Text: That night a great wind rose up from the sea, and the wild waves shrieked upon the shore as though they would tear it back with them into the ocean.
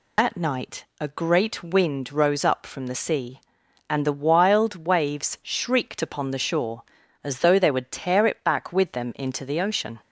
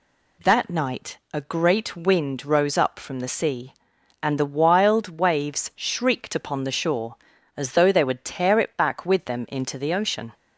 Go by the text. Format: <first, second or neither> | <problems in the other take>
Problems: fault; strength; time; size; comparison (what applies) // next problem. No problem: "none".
second | loses the start of "That"; at 0.1 s; 110 ms